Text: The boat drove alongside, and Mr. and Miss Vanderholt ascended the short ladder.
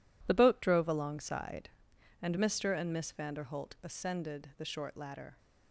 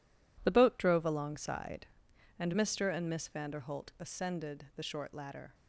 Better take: neither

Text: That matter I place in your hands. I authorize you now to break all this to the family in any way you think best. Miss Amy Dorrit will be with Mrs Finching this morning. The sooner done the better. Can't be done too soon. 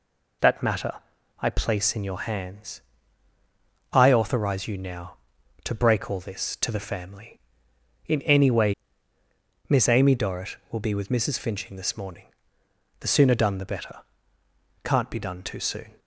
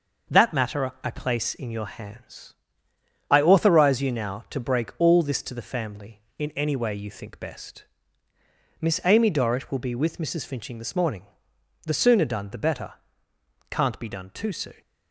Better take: second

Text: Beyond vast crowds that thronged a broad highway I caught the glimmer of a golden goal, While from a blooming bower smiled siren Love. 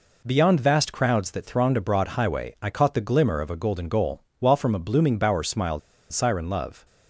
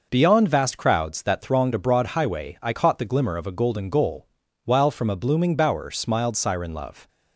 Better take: second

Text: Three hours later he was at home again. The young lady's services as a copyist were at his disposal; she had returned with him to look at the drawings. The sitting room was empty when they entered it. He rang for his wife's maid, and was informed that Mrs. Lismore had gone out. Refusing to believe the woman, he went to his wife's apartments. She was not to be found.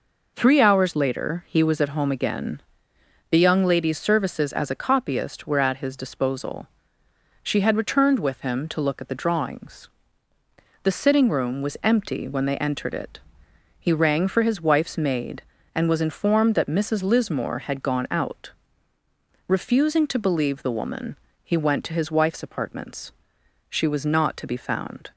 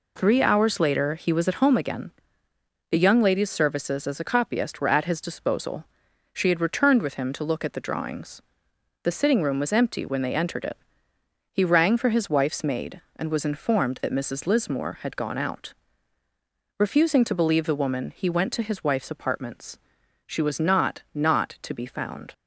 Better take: first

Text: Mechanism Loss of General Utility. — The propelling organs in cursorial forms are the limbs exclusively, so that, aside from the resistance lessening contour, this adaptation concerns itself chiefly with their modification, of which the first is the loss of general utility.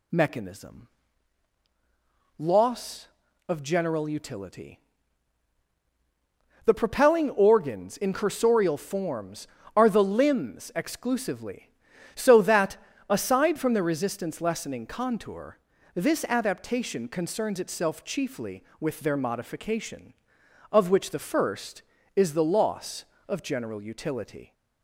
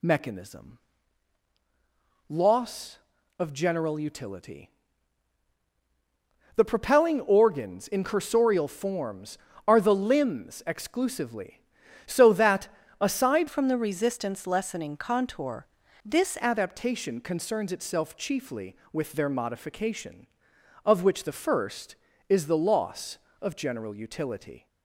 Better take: first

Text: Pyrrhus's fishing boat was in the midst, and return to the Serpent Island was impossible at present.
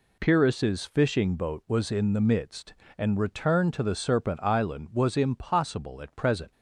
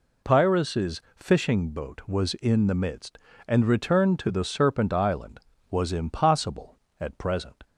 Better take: neither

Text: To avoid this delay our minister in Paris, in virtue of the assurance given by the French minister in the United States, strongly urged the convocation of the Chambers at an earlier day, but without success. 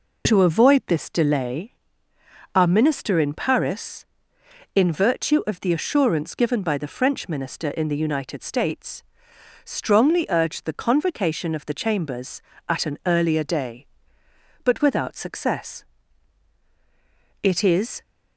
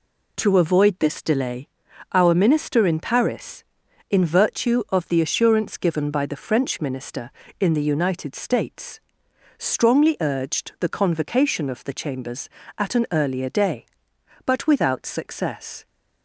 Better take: second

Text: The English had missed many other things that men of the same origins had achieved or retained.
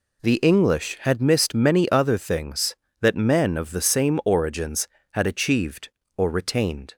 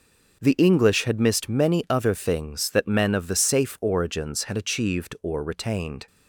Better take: first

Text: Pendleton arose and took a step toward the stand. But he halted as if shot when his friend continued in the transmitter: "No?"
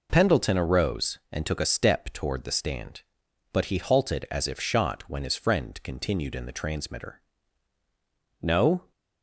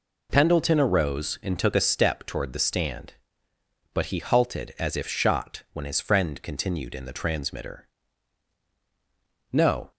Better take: neither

